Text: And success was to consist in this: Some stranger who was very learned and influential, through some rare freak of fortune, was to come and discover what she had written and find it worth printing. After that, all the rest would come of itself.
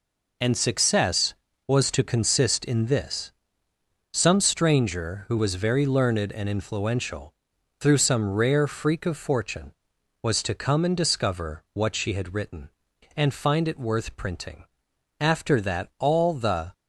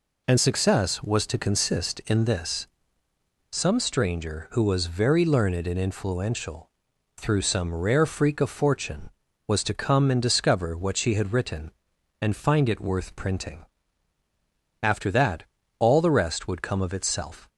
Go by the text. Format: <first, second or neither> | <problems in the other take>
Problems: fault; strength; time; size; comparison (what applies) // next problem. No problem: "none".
second | stops before "rest would come of itself"; at 16.7 s